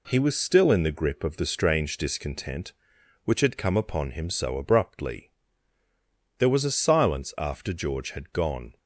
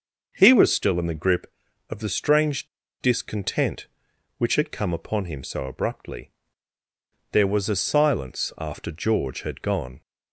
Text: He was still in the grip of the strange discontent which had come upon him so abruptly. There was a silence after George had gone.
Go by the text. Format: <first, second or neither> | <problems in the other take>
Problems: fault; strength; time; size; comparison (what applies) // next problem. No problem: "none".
first | starts louder than the rest; until 1.3 s; 6 dB // pauses between "strange" and "discontent"; slight; at 2.6 s; 0.32 s long